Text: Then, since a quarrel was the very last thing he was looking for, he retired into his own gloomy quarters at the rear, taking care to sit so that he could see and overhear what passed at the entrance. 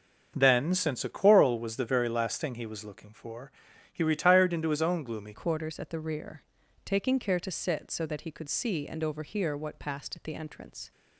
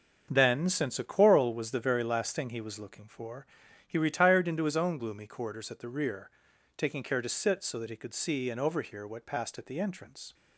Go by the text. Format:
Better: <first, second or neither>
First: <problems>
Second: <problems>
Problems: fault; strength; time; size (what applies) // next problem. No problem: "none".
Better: second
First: starts louder than the rest; until 1.3 s; 6.5 dB // changes voice at "quarters"; from 5.3 s on; 5.6 s long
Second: starts louder than the rest; until 1.3 s; 6.5 dB